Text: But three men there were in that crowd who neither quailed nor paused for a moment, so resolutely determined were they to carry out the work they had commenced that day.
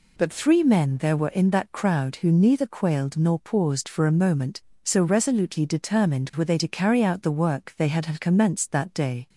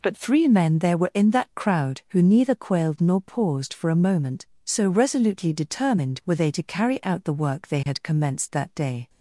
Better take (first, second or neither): second